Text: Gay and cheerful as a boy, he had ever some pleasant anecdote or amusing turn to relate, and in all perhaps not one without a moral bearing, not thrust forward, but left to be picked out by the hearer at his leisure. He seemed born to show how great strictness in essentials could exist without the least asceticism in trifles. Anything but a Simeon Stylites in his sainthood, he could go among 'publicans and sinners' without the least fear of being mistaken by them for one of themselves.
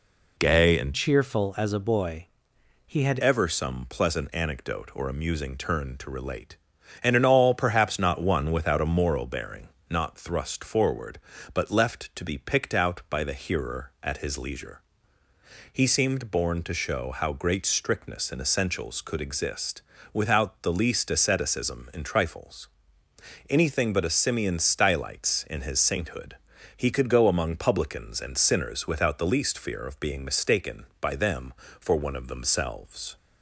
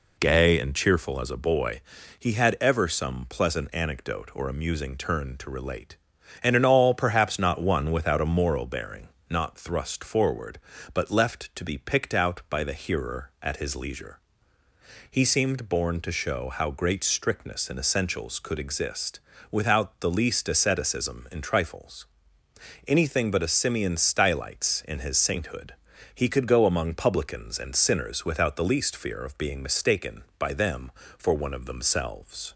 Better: second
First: changes voice from "cheerful" to "had"; from 0.9 to 3.1 s; 2.2 s long // pauses between "exist" and "without"; slight; at 19.8 s; 0.30 s long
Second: pauses between "exist" and "without"; slight; at 19.1 s; 0.30 s long

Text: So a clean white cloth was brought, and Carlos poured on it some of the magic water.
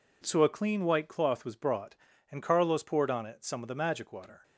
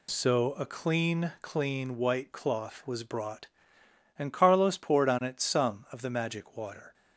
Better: first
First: none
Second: says "clean" twice; at 1.4 s

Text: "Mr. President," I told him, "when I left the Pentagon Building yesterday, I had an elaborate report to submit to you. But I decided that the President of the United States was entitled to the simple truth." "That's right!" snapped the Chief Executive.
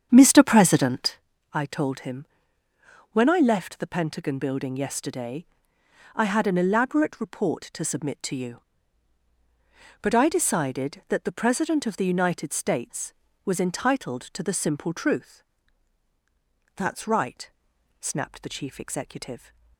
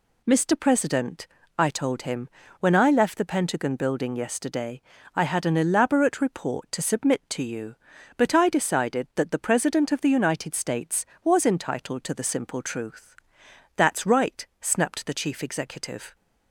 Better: second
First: starts louder than the rest; strong; until 1.2 s; 8 dB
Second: none

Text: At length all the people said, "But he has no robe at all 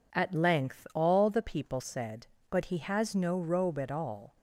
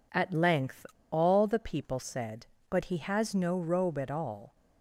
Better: first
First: none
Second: pauses between "length" and "all"; slight; at 0.8 s; 0.24 s long

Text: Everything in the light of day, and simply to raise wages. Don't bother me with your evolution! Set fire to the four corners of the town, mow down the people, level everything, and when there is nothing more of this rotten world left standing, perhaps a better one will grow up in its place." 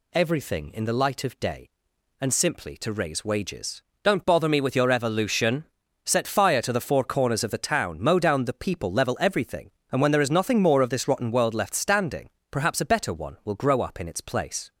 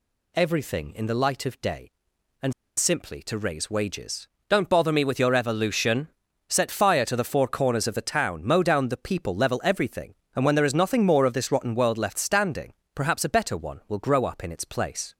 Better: first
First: none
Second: pauses between "and" and "simply"; slight; at 2.5 s; 0.24 s long

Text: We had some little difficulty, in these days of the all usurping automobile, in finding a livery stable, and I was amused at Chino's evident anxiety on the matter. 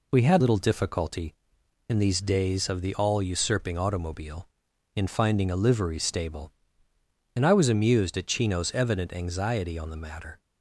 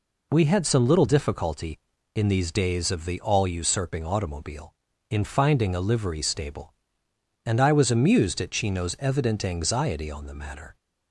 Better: second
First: skips "some"; at 0.4 s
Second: none

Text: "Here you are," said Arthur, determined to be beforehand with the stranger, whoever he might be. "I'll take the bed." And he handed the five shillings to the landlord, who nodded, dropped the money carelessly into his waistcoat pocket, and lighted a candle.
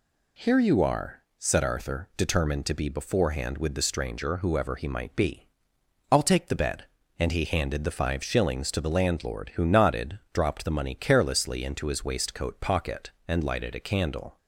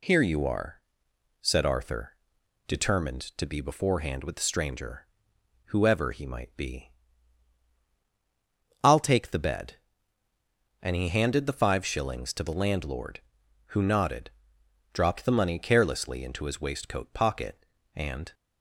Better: first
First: none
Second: stops before "lighted a candle"; at 18.3 s

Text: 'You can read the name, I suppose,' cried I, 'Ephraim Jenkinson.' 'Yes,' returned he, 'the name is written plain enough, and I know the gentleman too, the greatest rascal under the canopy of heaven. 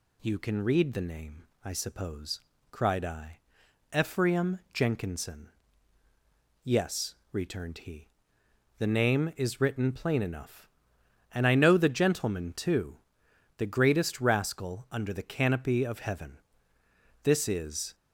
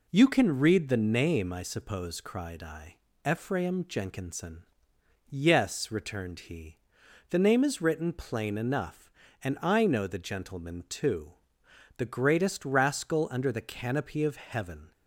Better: second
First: goes on to say "This is"; noticeable; from 17.2 s on; 0.72 s long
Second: none

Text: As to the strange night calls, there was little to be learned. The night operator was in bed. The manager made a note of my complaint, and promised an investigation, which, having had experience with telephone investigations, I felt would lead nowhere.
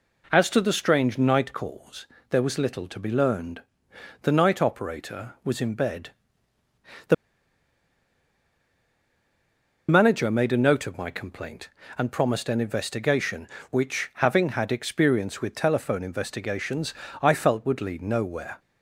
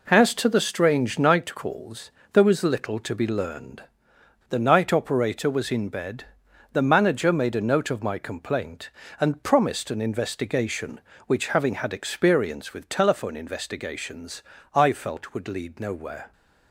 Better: second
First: pauses between "The" and "manager"; strong; at 7.1 s; 2.7 s long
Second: none

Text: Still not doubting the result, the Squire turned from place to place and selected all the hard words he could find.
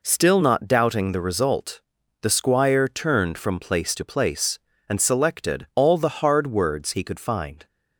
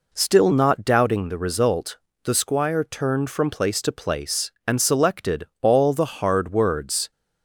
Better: first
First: none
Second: pauses between "selected" and "all"; slight; at 5.4 s; 0.16 s long // stops before "he could find"; at 7.1 s

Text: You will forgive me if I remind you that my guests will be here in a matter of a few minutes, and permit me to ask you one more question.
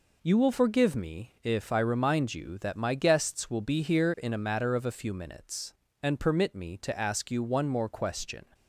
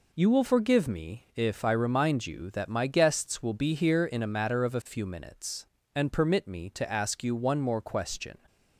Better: neither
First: none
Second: none

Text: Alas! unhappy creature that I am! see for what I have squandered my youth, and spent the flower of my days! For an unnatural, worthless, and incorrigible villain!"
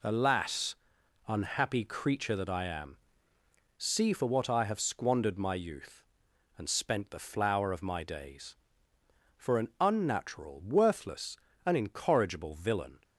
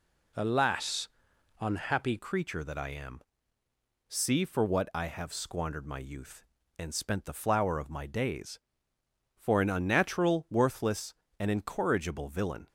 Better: first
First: none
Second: changes voice at "creature"; from 2.1 s on; 10.5 s long

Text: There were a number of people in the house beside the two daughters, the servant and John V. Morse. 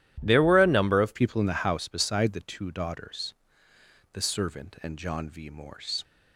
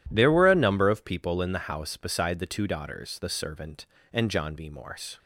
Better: second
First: changes voice at "people"; from 1.1 s on; 4.9 s long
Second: none

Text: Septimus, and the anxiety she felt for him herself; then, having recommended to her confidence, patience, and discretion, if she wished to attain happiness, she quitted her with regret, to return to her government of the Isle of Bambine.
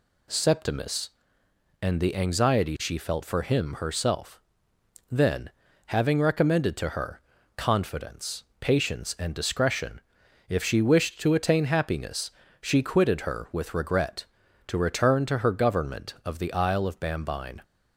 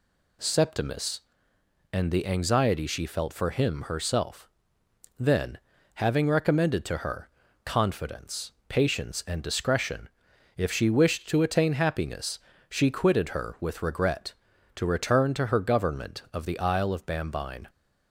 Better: neither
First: pauses between "her" and "confidence"; at 7.1 s; 0.38 s long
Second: pauses between "her" and "confidence"; at 7.2 s; 0.38 s long

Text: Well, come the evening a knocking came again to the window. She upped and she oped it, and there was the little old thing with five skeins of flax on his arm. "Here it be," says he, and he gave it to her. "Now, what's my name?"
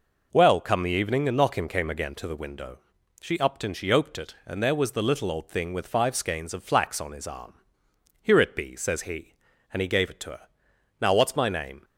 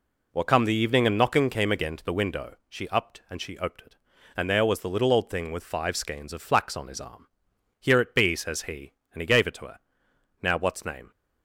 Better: first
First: none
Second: skips "my"; at 10.8 s

